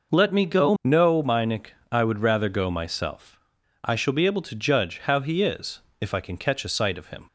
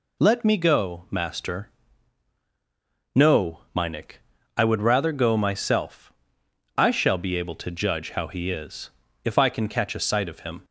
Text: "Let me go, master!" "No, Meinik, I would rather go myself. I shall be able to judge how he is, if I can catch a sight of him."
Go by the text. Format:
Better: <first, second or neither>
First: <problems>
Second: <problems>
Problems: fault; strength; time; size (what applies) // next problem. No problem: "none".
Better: second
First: skips "master"; at 0.7 s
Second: none